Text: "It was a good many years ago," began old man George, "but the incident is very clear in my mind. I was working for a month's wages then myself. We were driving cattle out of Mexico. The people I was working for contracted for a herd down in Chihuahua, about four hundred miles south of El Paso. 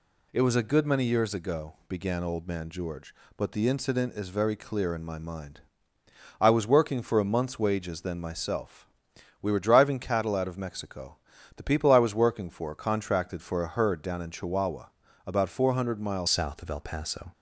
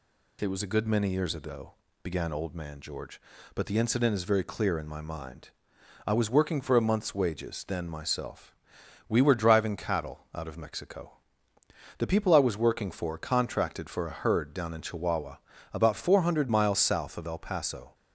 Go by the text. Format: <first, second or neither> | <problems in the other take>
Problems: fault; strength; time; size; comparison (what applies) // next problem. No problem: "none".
second | changes voice at "south"; from 16.2 s on; 1.1 s long